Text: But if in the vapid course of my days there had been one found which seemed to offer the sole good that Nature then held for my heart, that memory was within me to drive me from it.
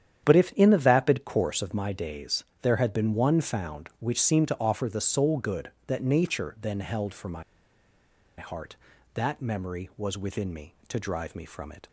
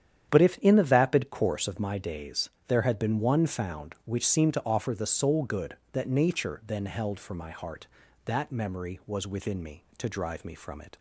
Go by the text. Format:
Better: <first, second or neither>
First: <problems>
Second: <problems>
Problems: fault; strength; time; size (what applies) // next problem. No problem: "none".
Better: second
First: starts louder than the rest; strong; until 1.2 s; 9.5 dB // pauses between "days" and "there"; slight; at 2.4 s; 0.16 s long // pauses between "my" and "heart"; noticeable; at 7.4 s; 0.94 s long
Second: starts louder than the rest; strong; until 1.3 s; 9.5 dB // pauses between "days" and "there"; slight; at 2.5 s; 0.16 s long